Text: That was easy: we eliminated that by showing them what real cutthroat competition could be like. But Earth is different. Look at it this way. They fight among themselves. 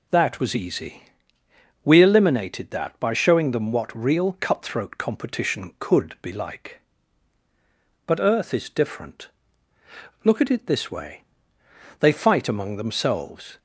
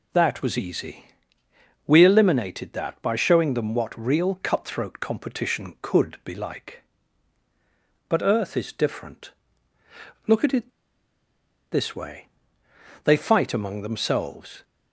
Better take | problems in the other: first | pauses between "it" and "this"; at 10.6 s; 1.0 s long

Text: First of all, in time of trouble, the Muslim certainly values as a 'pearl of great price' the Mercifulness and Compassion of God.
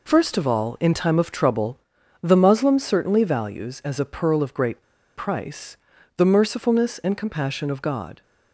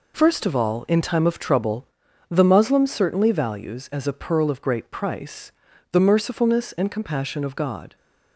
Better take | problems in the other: second | pauses between "great" and "price"; slight; at 4.8 s; 0.35 s long // pauses between "price" and "the"; at 5.7 s; 0.40 s long; also in the second

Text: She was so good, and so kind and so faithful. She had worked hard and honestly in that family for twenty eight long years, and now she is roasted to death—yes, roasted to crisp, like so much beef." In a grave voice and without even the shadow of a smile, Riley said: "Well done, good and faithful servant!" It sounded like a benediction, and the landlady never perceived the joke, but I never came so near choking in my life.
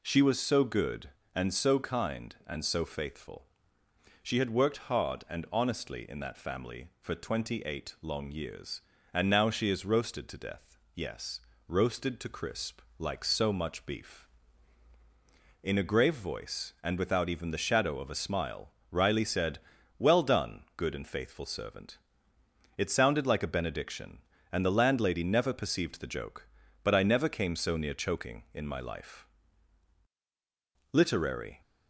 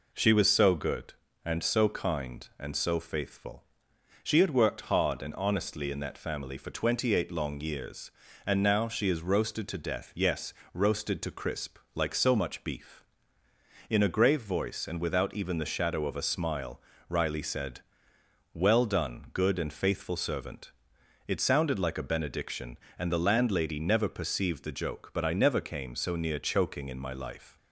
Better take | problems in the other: second | goes on to say "LITERARY"; noticeable; from 30.9 s on; 0.68 s long

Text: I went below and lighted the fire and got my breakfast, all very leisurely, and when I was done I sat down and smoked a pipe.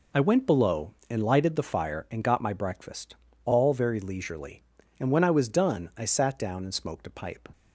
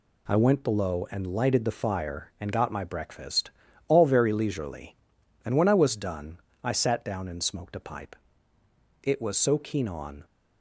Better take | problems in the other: first | pauses between "done" and "I"; slight; at 6.3 s; 0.26 s long // goes on to say "It was so keen on"; noticeable; from 9.0 s on; 1.2 s long

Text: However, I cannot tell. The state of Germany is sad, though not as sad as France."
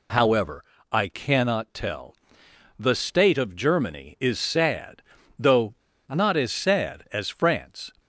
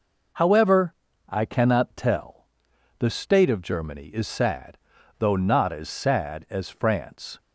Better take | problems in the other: second | pauses between "though" and "not"; slight; at 5.7 s; 0.35 s long

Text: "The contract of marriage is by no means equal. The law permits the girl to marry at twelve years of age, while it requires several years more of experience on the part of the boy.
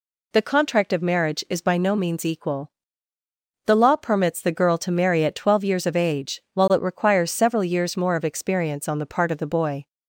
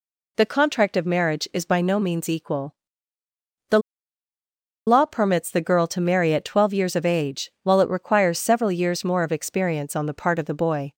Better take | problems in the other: first | pauses between "The" and "law"; at 3.7 s; 1.0 s long

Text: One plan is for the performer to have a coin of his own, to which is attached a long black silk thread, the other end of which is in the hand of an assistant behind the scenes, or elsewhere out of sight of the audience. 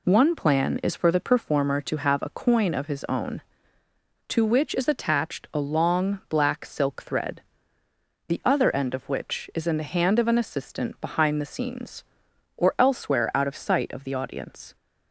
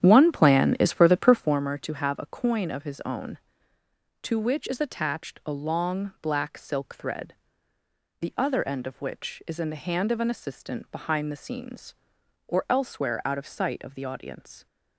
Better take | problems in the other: first | starts louder than the rest; strong; until 1.6 s; 10 dB

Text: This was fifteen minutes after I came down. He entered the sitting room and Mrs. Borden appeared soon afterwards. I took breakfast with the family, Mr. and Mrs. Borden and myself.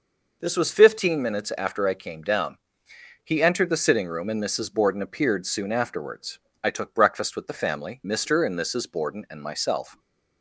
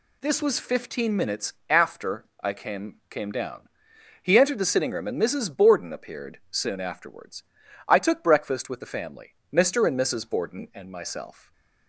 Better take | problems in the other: first | pauses between "after" and "I"; slight; at 2.2 s; 0.16 s long // says "came" twice; at 3.0 s // stays silent after the last word; slight; from 11.3 s on; 0.5 s long

